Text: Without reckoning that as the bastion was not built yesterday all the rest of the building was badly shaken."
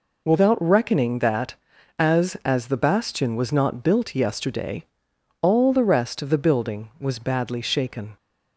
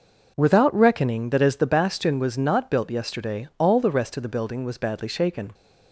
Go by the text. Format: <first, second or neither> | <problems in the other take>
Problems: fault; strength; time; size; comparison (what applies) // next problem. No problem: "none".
second | says "as" twice; at 2.4 s // pauses between "yesterday" and "all"; noticeable; at 4.8 s; 0.56 s long